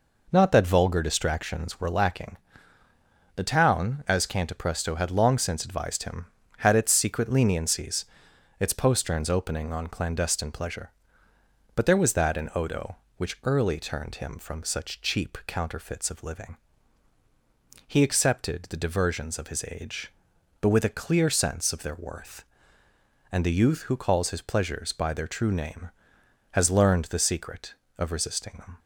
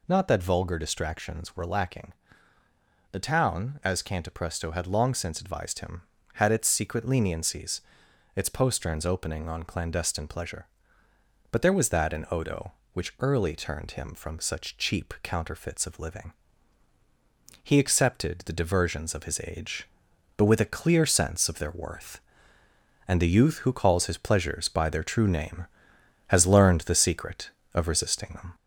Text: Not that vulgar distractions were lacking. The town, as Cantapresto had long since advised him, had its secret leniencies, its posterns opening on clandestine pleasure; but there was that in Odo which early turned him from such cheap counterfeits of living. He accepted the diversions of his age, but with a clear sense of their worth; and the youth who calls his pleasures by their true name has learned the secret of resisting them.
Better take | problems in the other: first | gets louder; slight; throughout; 2.5 dB

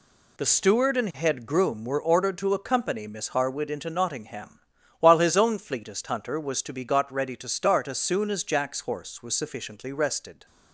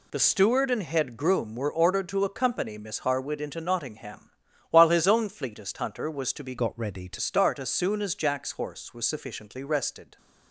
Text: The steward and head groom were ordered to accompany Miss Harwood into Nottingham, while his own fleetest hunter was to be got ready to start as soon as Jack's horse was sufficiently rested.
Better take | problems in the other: first | changes voice from "got" to "to"; from 6.5 to 7.1 s; 0.6 s long

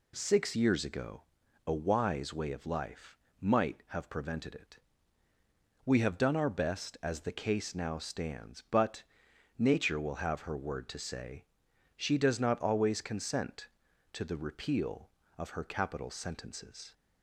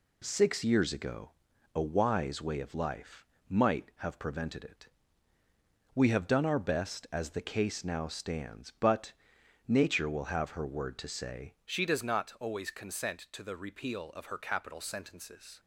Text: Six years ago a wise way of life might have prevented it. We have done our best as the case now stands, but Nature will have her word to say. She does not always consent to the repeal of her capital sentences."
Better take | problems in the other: first | pauses between "ago" and "a"; at 1.3 s; 0.44 s long; also in the first // pauses between "life" and "might"; slight; at 3.2 s; 0.22 s long; slight in the first // pauses between "but" and "Nature"; noticeable; at 9.1 s; 0.56 s long; noticeable in the first // changes voice at "She"; from 11.6 s on; 3.9 s long

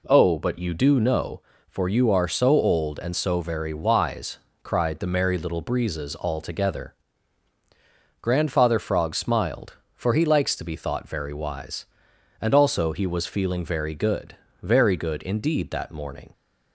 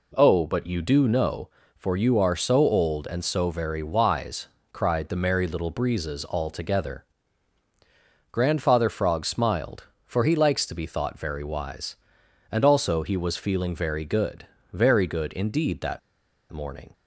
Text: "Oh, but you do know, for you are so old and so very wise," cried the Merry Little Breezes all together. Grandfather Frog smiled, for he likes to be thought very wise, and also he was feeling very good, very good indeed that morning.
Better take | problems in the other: first | pauses between "that" and "morning"; noticeable; at 15.9 s; 0.52 s long

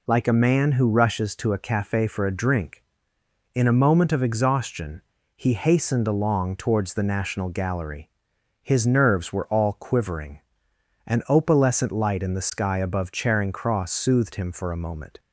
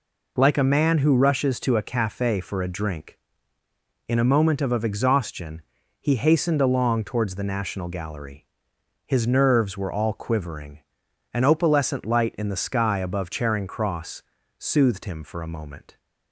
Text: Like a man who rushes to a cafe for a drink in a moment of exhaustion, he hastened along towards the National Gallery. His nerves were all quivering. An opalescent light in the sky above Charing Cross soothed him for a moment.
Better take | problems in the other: first | says "of" twice; at 4.7 s // pauses between "Cross" and "soothed"; slight; at 14.2 s; 0.34 s long

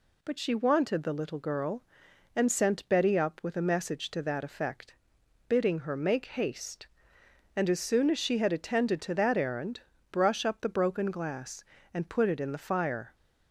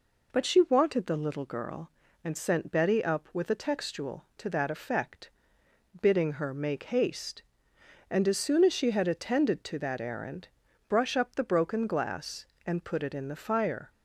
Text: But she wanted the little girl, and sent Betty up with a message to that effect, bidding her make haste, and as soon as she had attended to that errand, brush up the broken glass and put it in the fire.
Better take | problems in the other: first | says "textual" for "message"; at 3.5 s

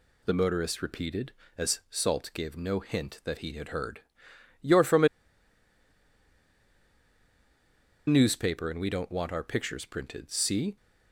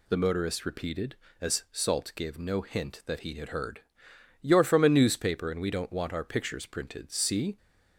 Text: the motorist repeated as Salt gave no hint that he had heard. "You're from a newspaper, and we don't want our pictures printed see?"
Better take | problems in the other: second | pauses between "a" and "newspaper"; strong; at 5.0 s; 2.9 s long

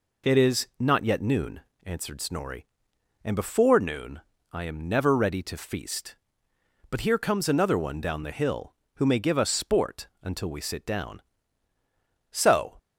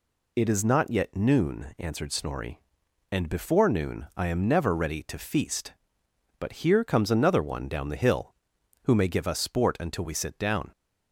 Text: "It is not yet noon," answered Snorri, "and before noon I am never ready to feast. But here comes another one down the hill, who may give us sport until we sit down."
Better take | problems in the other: second | pauses between "noon" and "I"; slight; at 4.2 s; 0.30 s long // goes on to say "So"; slight; from 12.3 s on; 0.46 s long

